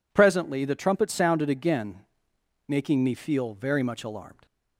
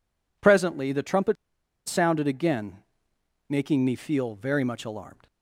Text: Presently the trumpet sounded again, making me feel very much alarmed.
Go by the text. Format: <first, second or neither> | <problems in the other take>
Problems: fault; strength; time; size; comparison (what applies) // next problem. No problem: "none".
first | pauses between "trumpet" and "sounded"; noticeable; at 1.3 s; 0.50 s long